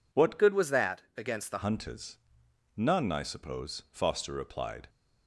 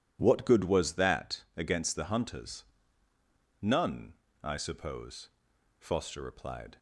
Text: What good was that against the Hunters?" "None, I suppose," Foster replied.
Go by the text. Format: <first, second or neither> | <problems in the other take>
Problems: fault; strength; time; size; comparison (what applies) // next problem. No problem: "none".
second | changes voice from "good" to "the"; from 0.3 to 1.6 s; 1.3 s long // pauses between "that" and "against"; slight; at 1.0 s; 0.16 s long